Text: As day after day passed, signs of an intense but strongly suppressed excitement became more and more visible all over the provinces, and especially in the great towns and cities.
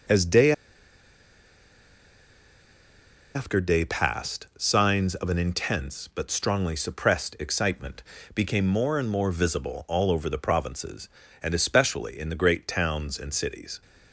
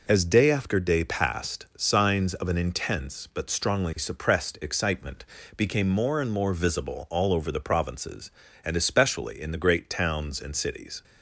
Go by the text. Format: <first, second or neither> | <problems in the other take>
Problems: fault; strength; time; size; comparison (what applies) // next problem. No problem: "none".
second | pauses between "day" and "after"; strong; at 0.5 s; 2.8 s long // pauses between "excitement" and "became"; slight; at 8.0 s; 0.32 s long; slight in the second